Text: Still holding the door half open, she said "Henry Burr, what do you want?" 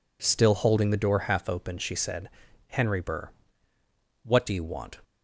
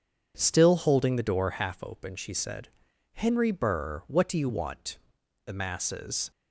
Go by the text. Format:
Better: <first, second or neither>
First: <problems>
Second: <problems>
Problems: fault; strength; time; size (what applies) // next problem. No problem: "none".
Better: first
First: pauses between "said" and "Henry"; at 2.2 s; 0.38 s long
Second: pauses between "said" and "Henry"; noticeable; at 2.6 s; 0.46 s long // goes on to say "The masses"; noticeable; from 5.4 s on; 0.86 s long